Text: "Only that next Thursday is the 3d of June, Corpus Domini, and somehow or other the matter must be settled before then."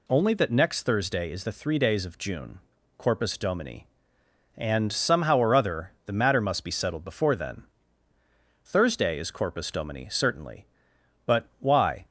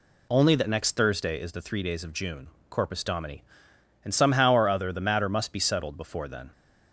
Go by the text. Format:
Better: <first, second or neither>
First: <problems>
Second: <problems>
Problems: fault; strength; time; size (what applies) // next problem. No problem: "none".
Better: second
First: goes on to say "Thursday is Corpus Domini certainly but why"; strong; from 8.6 s on; 3.4 s long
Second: none